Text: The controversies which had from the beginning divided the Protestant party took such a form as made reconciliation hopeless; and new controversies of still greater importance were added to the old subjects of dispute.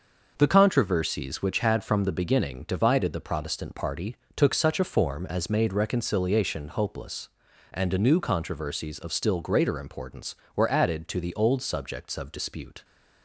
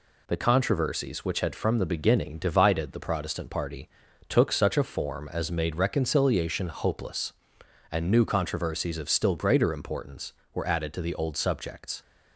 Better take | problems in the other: first | pauses between "party" and "took"; at 3.8 s; 0.38 s long; slight in the first // stops before "of dispute"; at 12.0 s

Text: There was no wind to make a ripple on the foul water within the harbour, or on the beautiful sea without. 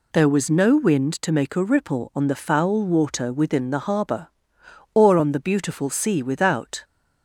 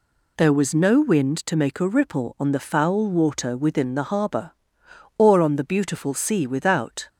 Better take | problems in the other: neither | none

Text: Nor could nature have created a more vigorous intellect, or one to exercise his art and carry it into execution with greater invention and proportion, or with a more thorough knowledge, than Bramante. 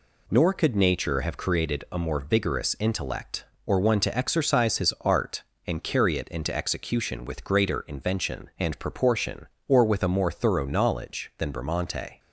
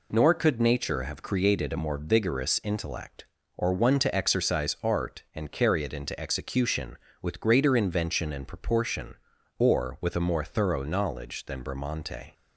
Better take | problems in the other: first | skips "his"; at 4.7 s

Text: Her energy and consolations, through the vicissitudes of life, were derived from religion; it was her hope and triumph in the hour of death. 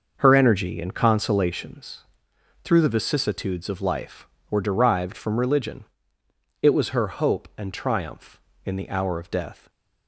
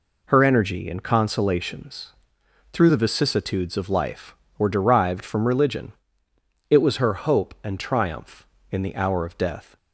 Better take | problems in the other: second | starts louder than the rest; noticeable; until 1.6 s; 6 dB // stays silent after the last word; slight; from 9.5 s on; 0.5 s long

